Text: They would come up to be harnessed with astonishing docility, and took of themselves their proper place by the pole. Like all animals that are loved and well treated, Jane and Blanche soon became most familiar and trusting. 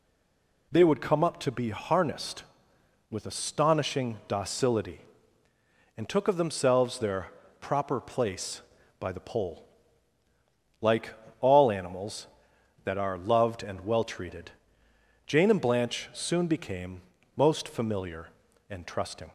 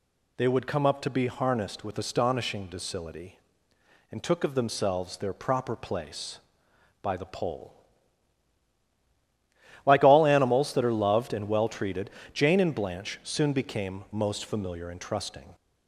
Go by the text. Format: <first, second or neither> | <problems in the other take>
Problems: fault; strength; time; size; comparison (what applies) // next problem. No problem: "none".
second | stays silent before the first word; slight; until 0.7 s; 0.7 s long // pauses between "their" and "proper"; slight; at 7.3 s; 0.28 s long // pauses between "Like" and "all"; slight; at 11.1 s; 0.26 s long // pauses between "became" and "most"; slight; at 17.0 s; 0.34 s long